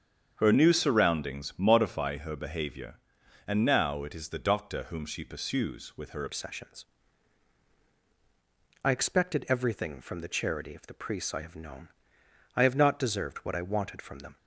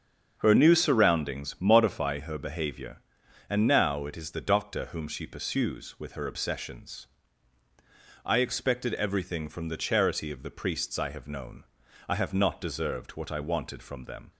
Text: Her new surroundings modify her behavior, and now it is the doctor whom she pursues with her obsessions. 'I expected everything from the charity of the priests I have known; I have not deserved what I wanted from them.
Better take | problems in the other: second | starts louder than the rest; strong; until 1.3 s; 7.5 dB; also in the second // changes voice at "obsessions"; from 6.2 s on; 8.1 s long

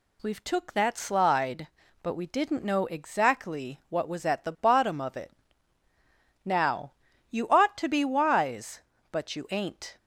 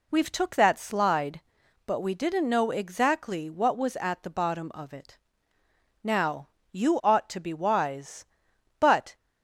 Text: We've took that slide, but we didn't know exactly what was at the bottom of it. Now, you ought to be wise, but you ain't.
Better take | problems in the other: first | stops before "you ain't"; at 9.1 s

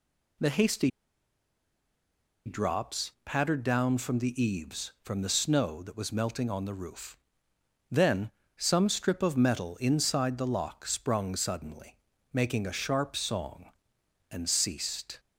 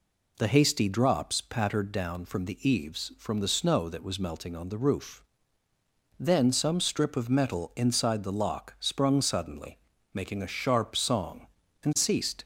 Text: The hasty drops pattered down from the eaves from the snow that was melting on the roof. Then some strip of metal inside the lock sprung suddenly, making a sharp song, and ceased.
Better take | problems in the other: second | pauses between "hasty" and "drops"; strong; at 0.9 s; 1.5 s long // pauses between "Then" and "some"; slight; at 8.2 s; 0.26 s long

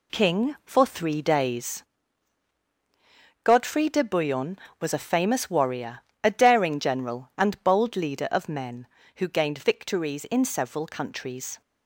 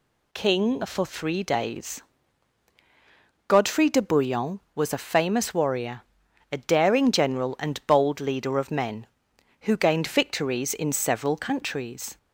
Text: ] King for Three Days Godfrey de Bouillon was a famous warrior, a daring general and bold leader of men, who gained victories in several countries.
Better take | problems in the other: second | gets quieter; strong; throughout; 7 dB // pauses between "Days" and "Godfrey"; strong; at 1.8 s; 1.6 s long; strong in the second

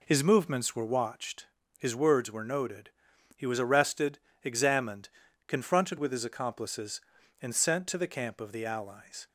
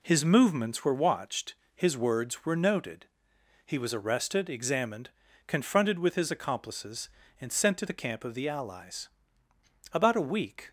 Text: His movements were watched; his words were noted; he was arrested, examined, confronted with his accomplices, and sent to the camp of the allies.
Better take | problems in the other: first | goes on to say "About a week"; noticeable; from 9.9 s on; 0.78 s long

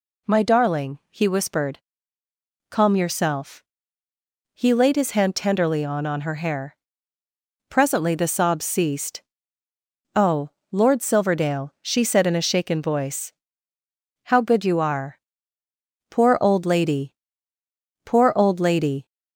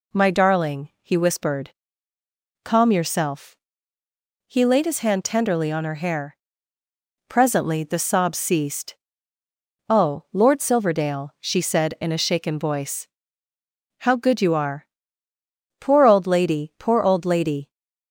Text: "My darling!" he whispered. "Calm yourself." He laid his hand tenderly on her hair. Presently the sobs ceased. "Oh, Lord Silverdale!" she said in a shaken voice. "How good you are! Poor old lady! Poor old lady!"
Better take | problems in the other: second | says "on" twice; at 6.0 s

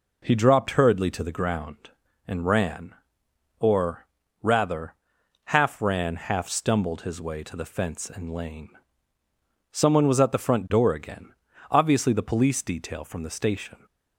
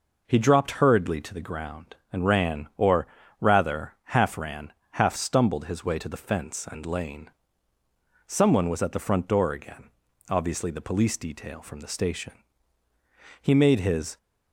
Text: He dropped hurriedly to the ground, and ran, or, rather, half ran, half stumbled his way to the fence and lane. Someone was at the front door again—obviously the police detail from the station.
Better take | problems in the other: first | goes on to say "He made his"; noticeable; from 13.4 s on; 0.76 s long

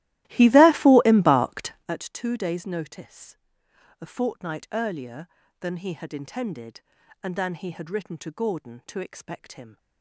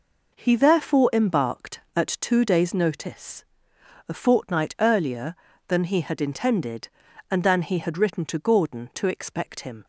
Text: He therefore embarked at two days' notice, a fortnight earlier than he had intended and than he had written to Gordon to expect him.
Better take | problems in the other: second | starts louder than the rest; strong; until 1.9 s; 15.5 dB

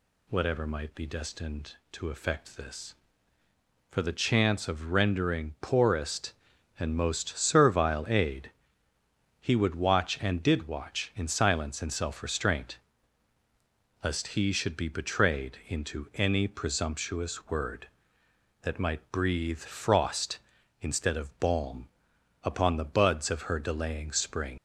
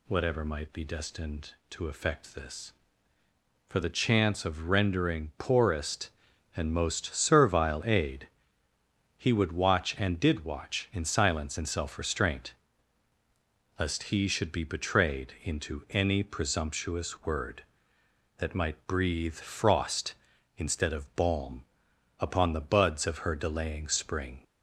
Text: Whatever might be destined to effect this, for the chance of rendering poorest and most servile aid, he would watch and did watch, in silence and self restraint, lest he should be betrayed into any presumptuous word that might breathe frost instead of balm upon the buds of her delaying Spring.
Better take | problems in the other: second | pauses between "balm" and "upon"; noticeable; at 21.8 s; 0.56 s long; noticeable in the second // leaves "Spring" unfinished; at 24.5 s; 85 ms

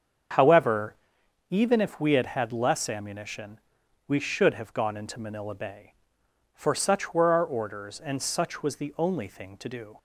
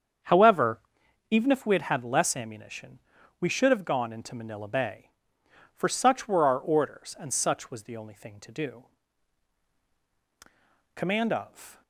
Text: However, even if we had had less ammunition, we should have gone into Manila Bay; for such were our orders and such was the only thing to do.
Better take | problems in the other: first | starts louder than the rest; strong; until 1.7 s; 7.5 dB; strong in the first // goes on to say "COMMAND OF"; noticeable; from 10.9 s on; 0.88 s long

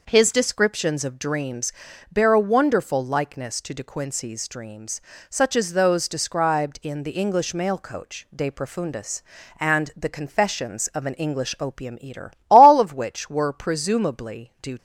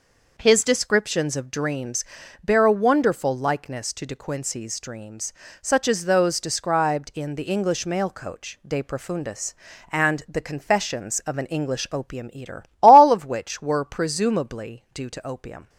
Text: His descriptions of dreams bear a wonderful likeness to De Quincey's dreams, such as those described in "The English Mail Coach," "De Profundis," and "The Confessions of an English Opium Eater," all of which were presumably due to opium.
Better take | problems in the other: second | pauses between "dreams" and "bear"; at 1.7 s; 0.38 s long; also in the second // stops before "to opium"; at 14.7 s

